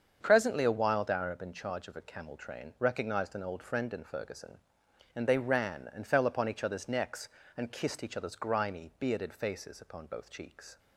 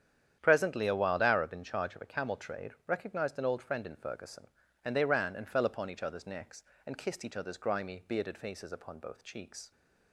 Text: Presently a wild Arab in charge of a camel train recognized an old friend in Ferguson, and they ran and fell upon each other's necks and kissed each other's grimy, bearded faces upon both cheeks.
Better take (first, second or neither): first